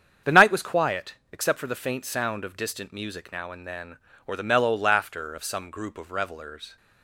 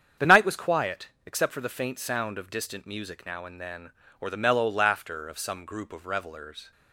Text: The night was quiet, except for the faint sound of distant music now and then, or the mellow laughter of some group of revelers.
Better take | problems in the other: neither | starts louder than the rest; strong; the same in both

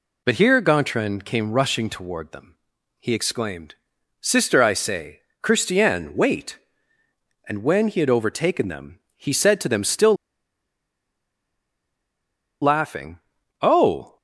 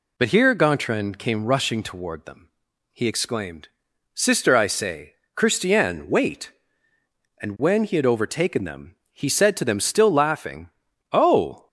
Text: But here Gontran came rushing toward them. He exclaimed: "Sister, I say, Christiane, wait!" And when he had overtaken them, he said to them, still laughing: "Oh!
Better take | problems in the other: second | pauses between "still" and "laughing"; strong; at 10.1 s; 2.4 s long

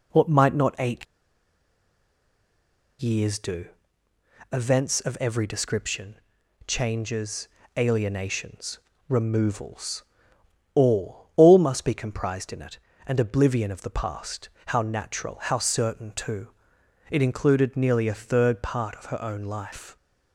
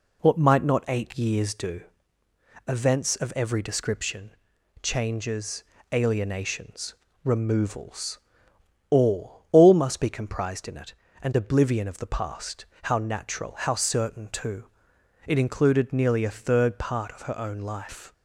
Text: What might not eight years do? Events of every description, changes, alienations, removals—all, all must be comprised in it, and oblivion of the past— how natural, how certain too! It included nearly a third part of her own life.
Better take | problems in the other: second | pauses between "eight" and "years"; strong; at 1.0 s; 1.9 s long

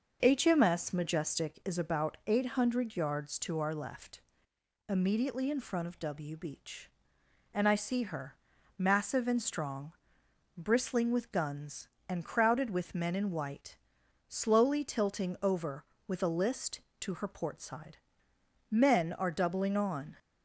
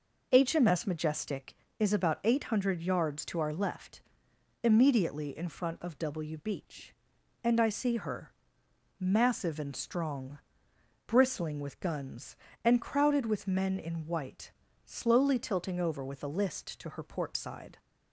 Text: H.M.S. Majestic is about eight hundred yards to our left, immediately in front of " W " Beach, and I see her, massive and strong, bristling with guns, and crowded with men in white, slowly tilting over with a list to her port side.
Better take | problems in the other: second | starts louder than the rest; until 1.2 s; 6 dB // goes on to say "Men are doubling on"; from 18.6 s on; 1.4 s long

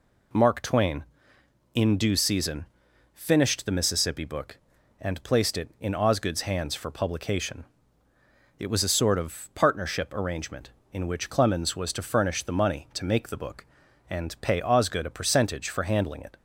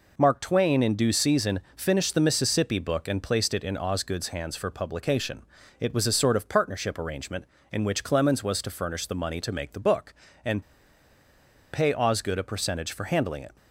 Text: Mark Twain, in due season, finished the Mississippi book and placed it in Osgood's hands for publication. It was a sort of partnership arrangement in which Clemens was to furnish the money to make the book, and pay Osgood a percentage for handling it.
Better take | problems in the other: first | pauses between "and" and "pay"; at 10.6 s; 1.1 s long

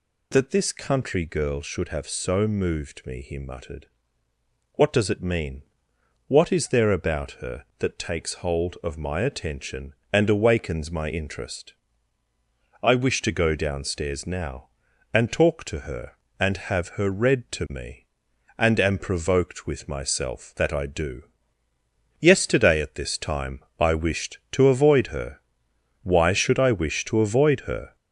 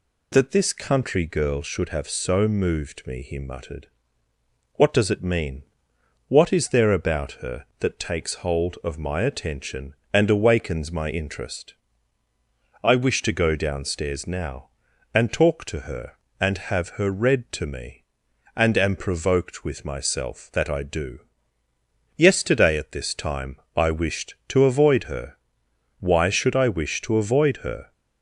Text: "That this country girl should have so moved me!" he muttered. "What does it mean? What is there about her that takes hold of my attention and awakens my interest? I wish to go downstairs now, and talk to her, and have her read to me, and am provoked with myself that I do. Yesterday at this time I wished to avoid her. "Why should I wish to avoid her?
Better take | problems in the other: second | gets louder; noticeable; throughout; 4.5 dB // pauses between "time" and "I"; slight; at 23.6 s; 0.16 s long; slight in the second

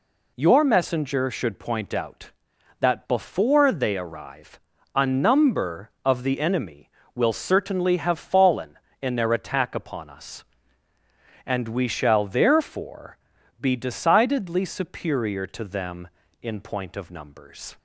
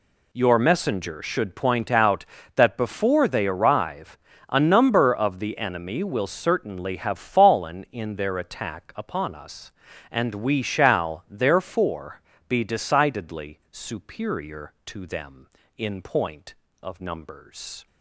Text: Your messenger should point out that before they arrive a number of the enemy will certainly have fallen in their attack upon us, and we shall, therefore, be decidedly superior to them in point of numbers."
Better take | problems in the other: neither | pauses between "arrive" and "a"; the same in both

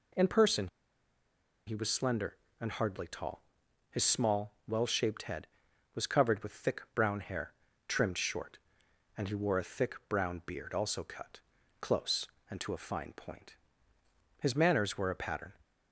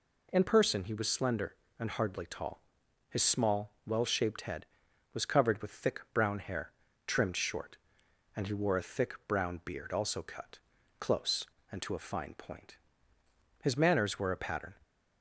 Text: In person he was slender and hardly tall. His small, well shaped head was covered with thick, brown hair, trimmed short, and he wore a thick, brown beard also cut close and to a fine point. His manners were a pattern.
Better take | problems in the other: second | pauses between "person" and "he"; at 0.6 s; 0.99 s long // pauses between "cut" and "close"; at 11.4 s; 0.40 s long; also in the second

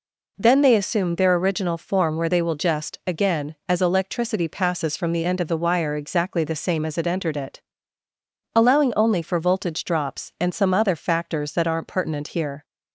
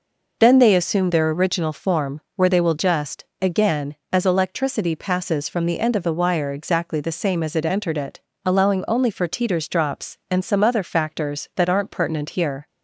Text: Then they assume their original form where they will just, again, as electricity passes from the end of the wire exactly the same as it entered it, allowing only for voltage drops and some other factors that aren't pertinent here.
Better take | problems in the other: first | pauses between "form" and "where"; slight; at 2.1 s; 0.16 s long // says "teeters" for "voltage"; at 9.2 s

